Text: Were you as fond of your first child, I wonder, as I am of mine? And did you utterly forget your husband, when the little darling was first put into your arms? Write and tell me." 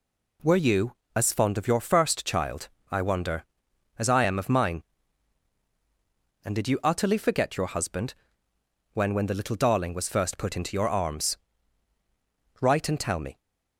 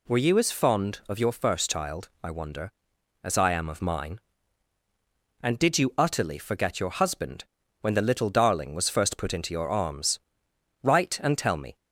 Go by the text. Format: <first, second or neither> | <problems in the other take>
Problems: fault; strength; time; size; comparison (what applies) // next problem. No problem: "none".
second | says "when" twice; at 9.1 s